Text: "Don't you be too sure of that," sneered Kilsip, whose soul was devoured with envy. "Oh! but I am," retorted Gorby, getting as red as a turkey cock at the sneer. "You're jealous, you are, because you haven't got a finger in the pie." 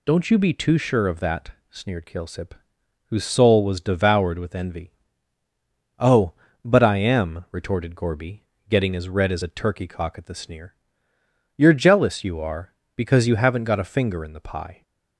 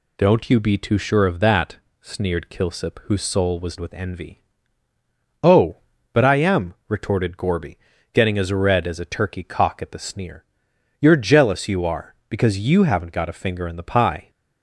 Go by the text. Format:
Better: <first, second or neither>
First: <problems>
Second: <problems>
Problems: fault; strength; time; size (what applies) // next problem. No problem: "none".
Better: first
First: none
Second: skips "devoured"; at 3.7 s